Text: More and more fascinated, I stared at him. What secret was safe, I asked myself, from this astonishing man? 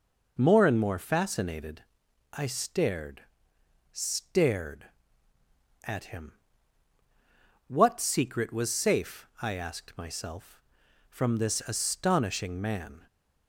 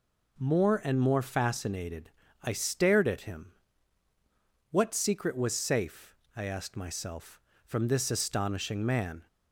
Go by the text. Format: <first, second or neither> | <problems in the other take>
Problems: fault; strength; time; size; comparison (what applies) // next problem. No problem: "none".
second | says "stared" twice; at 3.9 s